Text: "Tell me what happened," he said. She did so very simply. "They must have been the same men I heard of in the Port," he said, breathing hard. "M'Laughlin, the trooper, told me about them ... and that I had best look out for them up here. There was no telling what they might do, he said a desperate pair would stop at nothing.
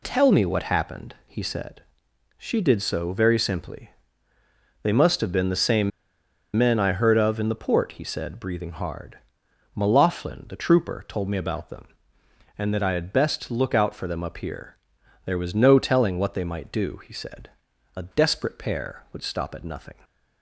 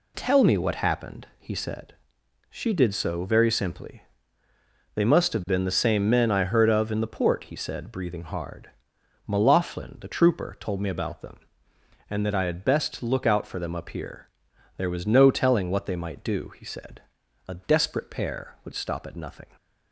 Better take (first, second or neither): second